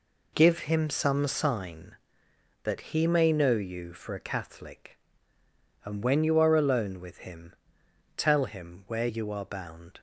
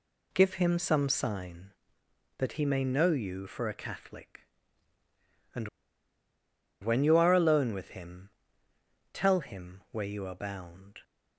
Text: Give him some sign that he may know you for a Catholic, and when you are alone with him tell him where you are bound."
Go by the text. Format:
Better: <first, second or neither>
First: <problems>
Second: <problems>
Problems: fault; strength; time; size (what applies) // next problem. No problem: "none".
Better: first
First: pauses between "him" and "tell"; noticeable; at 7.5 s; 0.64 s long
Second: pauses between "and" and "when"; at 5.6 s; 1.1 s long // pauses between "him" and "tell"; noticeable; at 8.2 s; 0.82 s long